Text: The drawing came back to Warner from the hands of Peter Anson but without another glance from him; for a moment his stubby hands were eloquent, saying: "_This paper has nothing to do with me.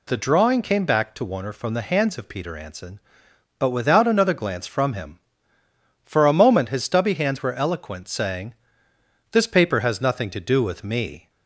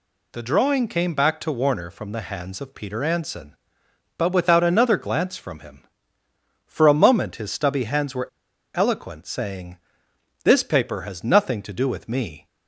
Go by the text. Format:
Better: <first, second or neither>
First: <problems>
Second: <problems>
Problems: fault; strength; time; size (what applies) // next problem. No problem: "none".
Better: first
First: none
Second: pauses between "were" and "eloquent"; noticeable; at 8.2 s; 0.47 s long